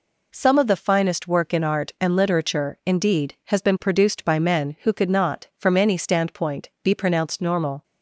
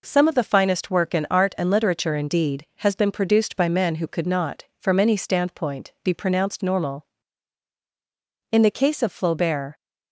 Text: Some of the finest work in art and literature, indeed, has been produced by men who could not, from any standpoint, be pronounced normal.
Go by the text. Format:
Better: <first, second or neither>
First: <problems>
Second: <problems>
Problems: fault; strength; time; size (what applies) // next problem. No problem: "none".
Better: first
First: none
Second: goes on to say "In the case of Flaubert"; noticeable; from 8.5 s on; 1.2 s long